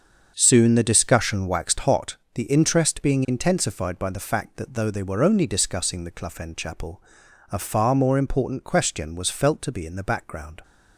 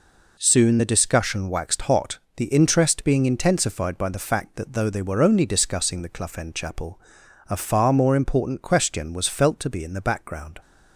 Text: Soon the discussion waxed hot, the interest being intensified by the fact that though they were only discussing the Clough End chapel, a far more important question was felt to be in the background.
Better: second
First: starts louder than the rest; until 2.0 s; 6.5 dB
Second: none

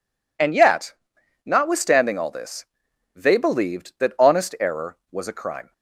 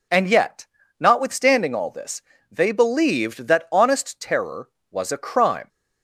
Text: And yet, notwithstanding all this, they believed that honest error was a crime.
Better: first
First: none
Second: says "terror" for "error"; at 4.2 s

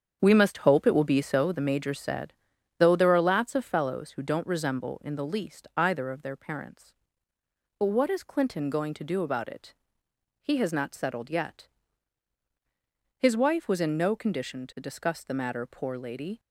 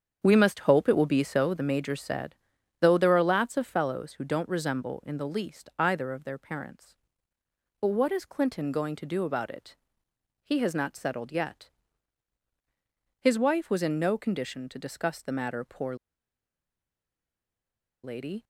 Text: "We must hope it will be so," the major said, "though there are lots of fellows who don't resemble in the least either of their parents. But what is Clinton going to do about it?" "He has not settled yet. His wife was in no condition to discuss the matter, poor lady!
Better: first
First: starts louder than the rest; strong; until 1.2 s; 7.5 dB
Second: starts louder than the rest; strong; until 1.2 s; 7.5 dB // pauses between "poor" and "lady"; strong; at 15.9 s; 2.0 s long

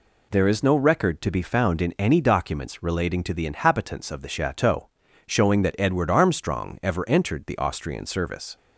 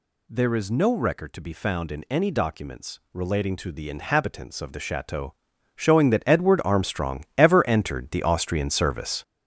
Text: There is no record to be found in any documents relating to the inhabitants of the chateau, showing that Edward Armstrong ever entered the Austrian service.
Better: first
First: none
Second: gets louder; strong; throughout; 8 dB

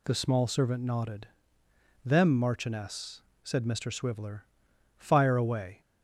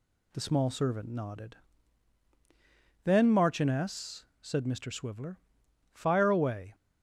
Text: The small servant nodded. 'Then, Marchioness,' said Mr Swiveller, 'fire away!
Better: second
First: says "Them" for "Then"; at 2.0 s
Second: none

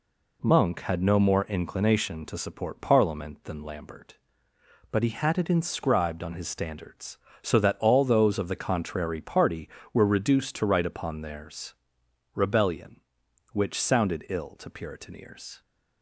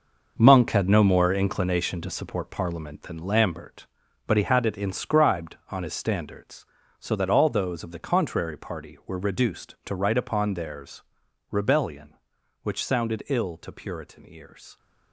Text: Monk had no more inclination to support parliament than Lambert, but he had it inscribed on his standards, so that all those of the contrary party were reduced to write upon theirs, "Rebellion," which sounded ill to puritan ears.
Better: first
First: none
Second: gets quieter; strong; throughout; 10.5 dB

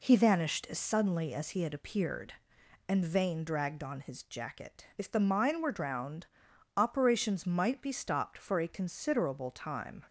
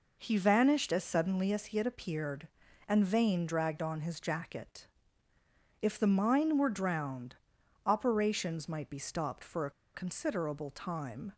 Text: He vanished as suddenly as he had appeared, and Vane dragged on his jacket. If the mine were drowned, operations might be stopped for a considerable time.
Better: first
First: none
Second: pauses between "a" and "considerable"; slight; at 9.7 s; 0.23 s long

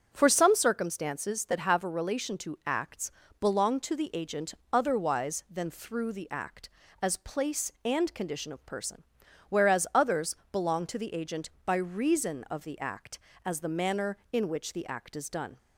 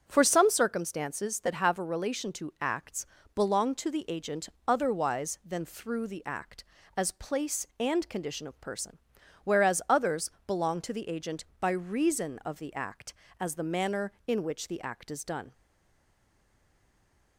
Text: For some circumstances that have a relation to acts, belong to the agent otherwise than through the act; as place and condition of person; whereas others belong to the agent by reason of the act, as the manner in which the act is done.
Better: first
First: starts louder than the rest; until 1.1 s; 6.5 dB // pauses between "agent" and "otherwise"; slight; at 4.5 s; 0.18 s long // pauses between "others" and "belong"; slight; at 10.3 s; 0.16 s long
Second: starts louder than the rest; until 1.0 s; 6.5 dB // pauses between "agent" and "otherwise"; slight; at 4.4 s; 0.18 s long // pauses between "others" and "belong"; slight; at 10.3 s; 0.16 s long // stays silent after the last word; noticeable; from 15.5 s on; 1.8 s long

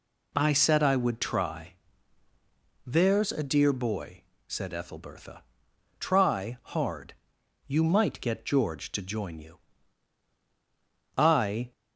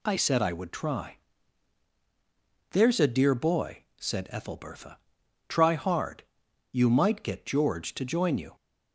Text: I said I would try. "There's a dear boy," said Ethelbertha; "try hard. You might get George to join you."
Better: second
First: goes on to say "I"; from 11.1 s on; 0.54 s long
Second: none

